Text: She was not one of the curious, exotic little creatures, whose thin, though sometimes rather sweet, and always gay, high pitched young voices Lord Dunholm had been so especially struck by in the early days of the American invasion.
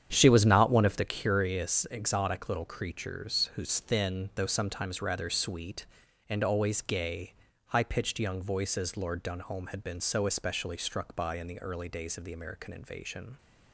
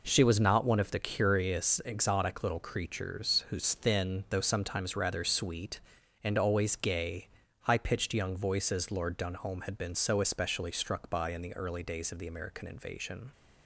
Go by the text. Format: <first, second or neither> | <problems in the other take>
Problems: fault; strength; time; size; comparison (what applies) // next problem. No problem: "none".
second | starts louder than the rest; strong; until 1.2 s; 9 dB